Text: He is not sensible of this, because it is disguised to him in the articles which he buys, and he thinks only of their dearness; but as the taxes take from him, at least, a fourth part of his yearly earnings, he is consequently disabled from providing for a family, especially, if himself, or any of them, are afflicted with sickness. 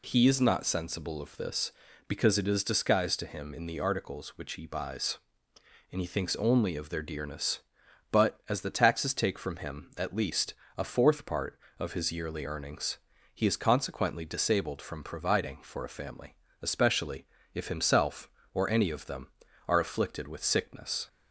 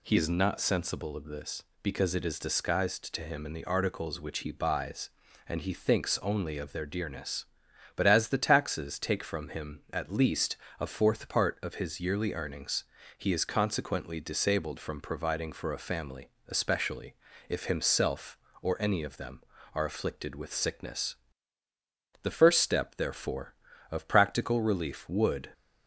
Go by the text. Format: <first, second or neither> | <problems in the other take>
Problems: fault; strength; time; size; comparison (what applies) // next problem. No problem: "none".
first | goes on to say "The first step therefore of practical relief would"; strong; from 22.2 s on; 3.2 s long